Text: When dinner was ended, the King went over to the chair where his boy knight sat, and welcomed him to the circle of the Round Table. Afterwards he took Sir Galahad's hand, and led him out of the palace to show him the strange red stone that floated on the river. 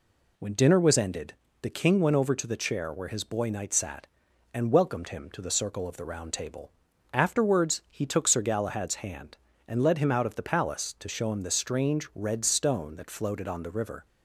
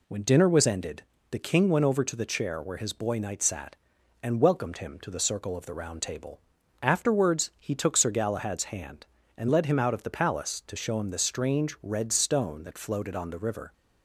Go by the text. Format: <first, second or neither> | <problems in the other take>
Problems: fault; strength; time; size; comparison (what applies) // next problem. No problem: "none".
neither | none